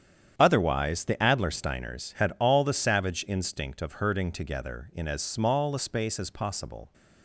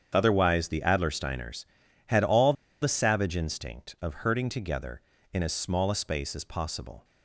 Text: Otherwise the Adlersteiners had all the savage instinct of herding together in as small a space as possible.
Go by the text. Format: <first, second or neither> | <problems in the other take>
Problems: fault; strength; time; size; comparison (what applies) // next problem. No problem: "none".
first | starts louder than the rest; strong; until 1.1 s; 8 dB; strong in the first // pauses between "all" and "the"; slight; at 2.5 s; 0.28 s long